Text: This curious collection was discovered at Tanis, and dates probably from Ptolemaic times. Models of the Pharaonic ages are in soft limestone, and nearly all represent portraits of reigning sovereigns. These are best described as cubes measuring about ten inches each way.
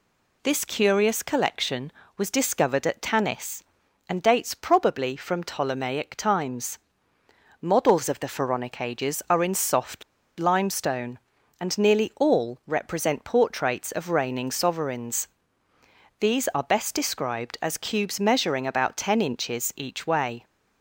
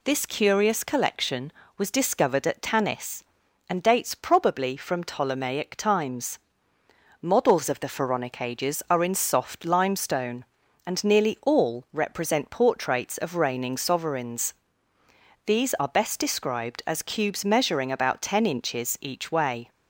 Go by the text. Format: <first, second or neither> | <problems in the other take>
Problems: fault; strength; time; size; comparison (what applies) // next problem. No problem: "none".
second | pauses between "soft" and "limestone"; at 10.0 s; 0.36 s long